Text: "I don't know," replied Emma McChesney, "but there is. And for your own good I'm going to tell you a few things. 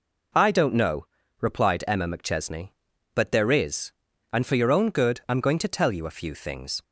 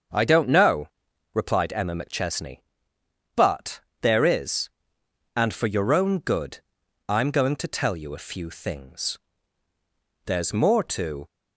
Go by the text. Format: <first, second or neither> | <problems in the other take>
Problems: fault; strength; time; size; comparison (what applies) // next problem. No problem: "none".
first | starts louder than the rest; until 1.5 s; 6.5 dB // pauses between "but" and "there"; slight; at 3.8 s; 0.20 s long // pauses between "good" and "I'm"; noticeable; at 6.5 s; 0.50 s long // goes on to say "There's more to"; noticeable; from 10.2 s on; 1.0 s long